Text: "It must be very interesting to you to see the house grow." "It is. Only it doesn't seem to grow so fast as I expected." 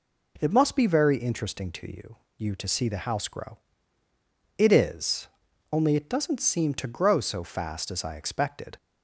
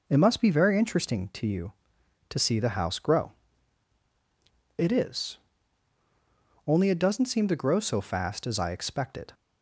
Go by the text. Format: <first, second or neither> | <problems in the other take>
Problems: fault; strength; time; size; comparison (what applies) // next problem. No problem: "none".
second | says "you" twice; at 2.3 s